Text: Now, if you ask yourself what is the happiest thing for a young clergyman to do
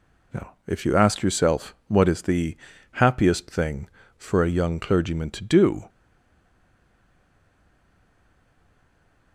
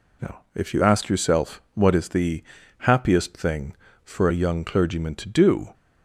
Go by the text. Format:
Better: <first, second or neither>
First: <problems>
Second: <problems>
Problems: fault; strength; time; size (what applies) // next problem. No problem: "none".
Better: second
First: pauses between "the" and "happiest"; slight; at 2.5 s; 0.36 s long // stays silent after the last word; strong; from 5.8 s on; 3.5 s long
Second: pauses between "the" and "happiest"; slight; at 2.4 s; 0.36 s long